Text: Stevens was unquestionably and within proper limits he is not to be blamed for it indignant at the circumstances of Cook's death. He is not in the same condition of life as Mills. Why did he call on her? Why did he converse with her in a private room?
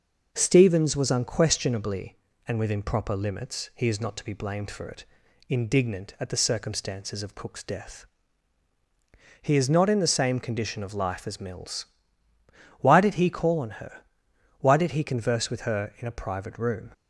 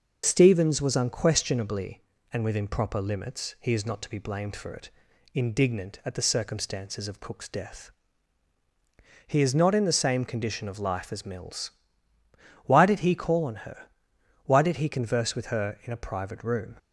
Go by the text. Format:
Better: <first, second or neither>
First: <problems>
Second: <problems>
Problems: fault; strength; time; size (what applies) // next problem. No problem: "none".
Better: first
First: pauses between "it" and "indignant"; noticeable; at 5.0 s; 0.46 s long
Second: loses the start of "Stevens"; at 0.2 s; 45 ms // pauses between "it" and "indignant"; noticeable; at 4.8 s; 0.46 s long